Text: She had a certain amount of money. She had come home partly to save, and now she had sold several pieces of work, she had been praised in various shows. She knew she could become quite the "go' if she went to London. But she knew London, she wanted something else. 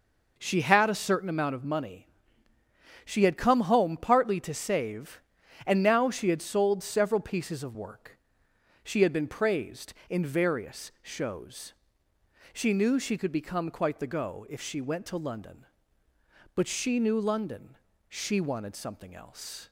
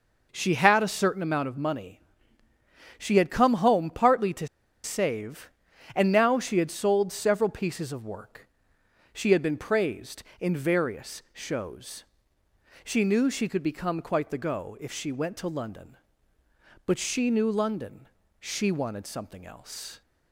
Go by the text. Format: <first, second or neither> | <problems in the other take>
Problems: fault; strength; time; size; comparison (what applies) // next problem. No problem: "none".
first | pauses between "to" and "save"; at 4.4 s; 0.36 s long